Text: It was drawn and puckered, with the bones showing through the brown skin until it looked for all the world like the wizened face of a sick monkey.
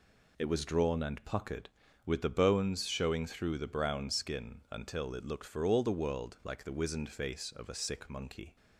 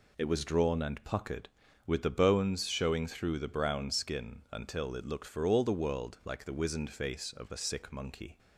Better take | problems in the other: neither | none

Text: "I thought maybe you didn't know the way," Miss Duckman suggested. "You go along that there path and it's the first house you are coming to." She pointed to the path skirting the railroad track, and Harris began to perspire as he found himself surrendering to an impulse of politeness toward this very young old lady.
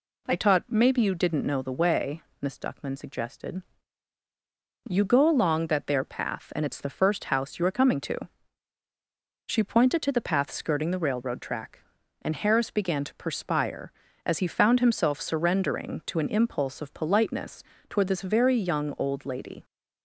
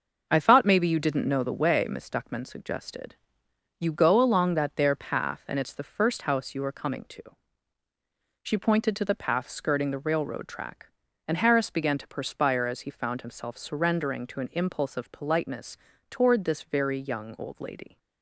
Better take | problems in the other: second | says "taught" for "thought"; at 0.3 s // pauses between "politeness" and "toward"; slight; at 17.6 s; 0.24 s long; slight in the second

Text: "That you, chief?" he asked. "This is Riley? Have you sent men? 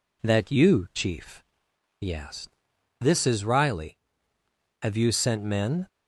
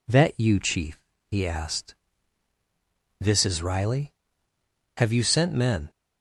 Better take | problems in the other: neither | none

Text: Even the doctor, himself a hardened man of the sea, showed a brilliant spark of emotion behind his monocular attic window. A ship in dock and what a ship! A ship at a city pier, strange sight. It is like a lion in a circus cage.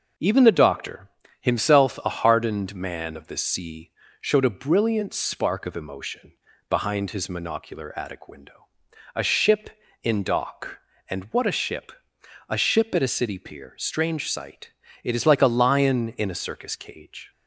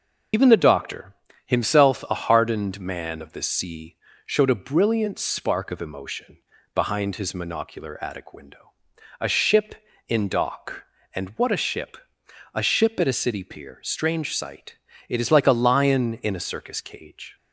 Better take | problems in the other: first | loses the start of "Even"; at 0.3 s; 100 ms // pauses between "emotion" and "behind"; at 6.3 s; 0.38 s long; also in the first

